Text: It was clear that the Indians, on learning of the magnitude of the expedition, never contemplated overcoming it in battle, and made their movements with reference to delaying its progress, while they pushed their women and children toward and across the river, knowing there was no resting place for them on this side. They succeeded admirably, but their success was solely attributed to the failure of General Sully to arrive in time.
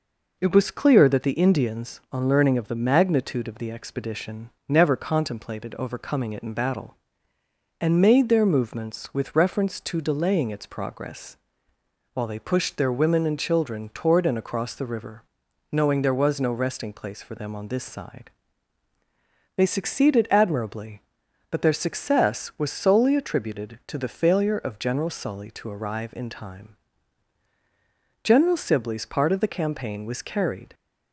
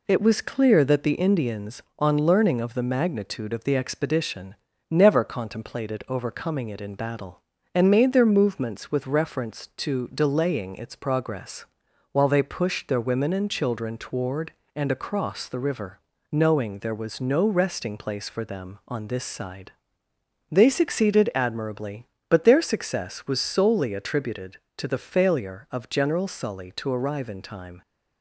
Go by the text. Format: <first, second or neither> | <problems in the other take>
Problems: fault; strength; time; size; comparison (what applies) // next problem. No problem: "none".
second | goes on to say "General Sibley's part of the campaign was carried"; strong; from 28.2 s on; 2.5 s long